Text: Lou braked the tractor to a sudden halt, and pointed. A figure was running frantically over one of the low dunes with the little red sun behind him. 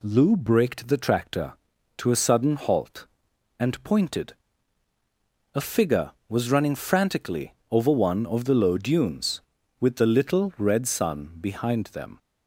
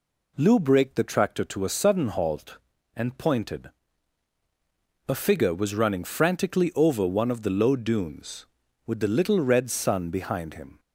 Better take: second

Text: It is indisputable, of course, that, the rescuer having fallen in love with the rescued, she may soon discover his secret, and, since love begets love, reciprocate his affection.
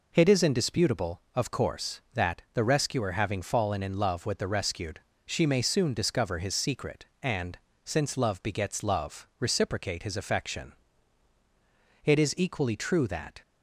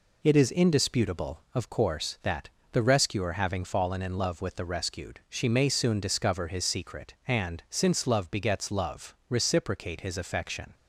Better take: second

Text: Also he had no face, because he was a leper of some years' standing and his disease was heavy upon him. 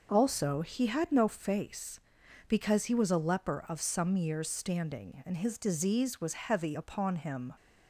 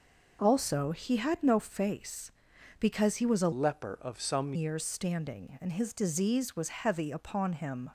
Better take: first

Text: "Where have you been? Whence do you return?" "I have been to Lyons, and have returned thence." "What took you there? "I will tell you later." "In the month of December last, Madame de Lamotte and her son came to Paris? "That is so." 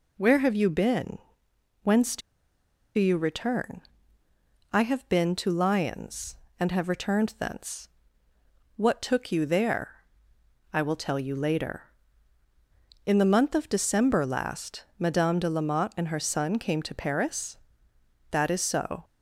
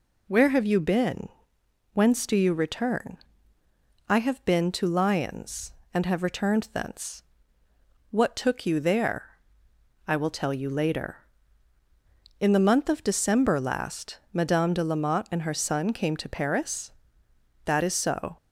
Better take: second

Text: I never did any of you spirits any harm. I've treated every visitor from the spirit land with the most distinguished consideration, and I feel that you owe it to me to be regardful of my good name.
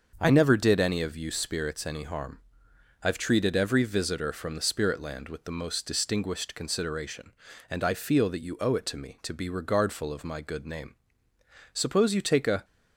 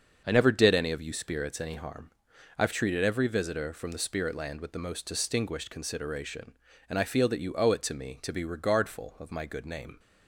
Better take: second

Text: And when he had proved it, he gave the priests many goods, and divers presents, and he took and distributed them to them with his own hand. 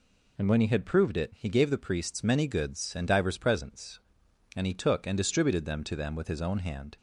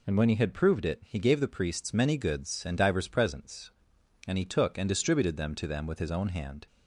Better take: neither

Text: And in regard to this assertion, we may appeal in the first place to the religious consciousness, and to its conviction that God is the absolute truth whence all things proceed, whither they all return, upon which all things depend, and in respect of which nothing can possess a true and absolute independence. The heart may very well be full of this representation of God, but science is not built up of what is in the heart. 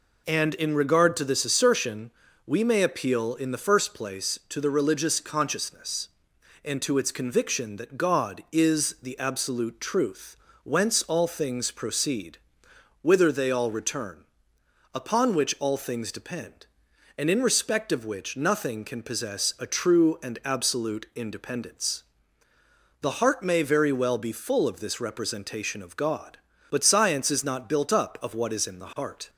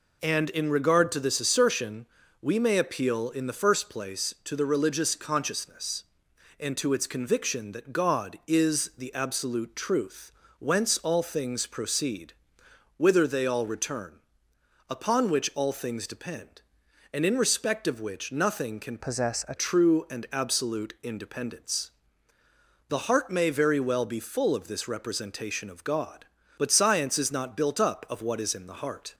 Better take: first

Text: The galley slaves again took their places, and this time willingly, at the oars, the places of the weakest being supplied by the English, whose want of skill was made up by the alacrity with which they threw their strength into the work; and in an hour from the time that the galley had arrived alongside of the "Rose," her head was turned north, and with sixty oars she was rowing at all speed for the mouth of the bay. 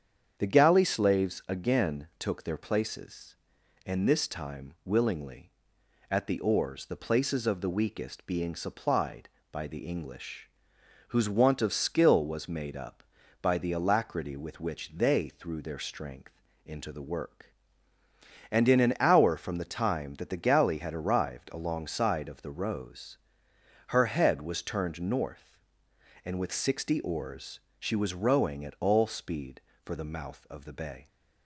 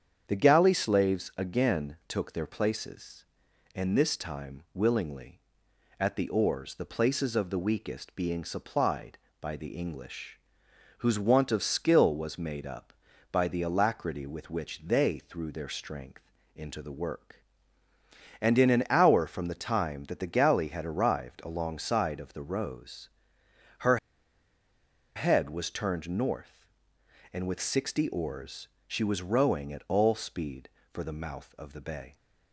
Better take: first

